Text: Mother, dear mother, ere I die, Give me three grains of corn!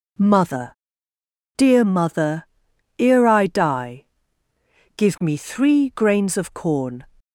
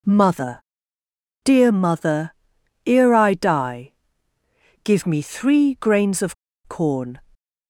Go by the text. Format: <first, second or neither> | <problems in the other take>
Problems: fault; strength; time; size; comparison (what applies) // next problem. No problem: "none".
first | pauses between "of" and "corn"; slight; at 6.3 s; 0.31 s long